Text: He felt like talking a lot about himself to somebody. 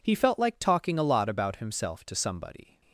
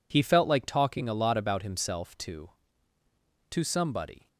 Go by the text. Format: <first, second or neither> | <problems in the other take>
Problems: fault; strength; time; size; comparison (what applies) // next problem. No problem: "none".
first | says "to" twice; at 3.4 s